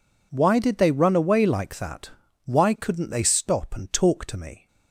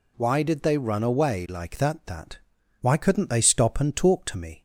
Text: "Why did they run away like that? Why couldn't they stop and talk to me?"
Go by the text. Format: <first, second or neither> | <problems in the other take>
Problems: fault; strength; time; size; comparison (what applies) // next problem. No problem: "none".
first | says "that" twice; at 2.0 s